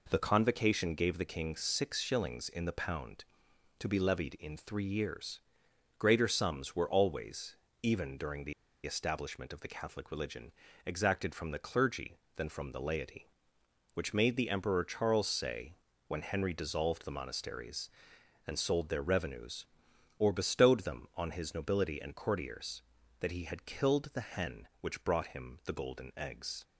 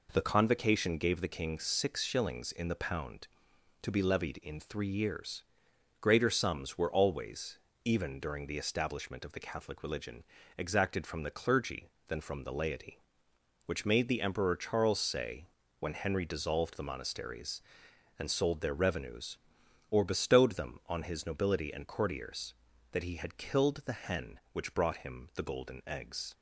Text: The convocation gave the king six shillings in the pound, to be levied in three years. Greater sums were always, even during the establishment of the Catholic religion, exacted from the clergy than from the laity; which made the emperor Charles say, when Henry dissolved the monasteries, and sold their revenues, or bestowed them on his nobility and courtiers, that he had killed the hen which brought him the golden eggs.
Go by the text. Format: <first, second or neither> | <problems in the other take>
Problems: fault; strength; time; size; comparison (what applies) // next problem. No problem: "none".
second | pauses between "the" and "establishment"; slight; at 8.5 s; 0.32 s long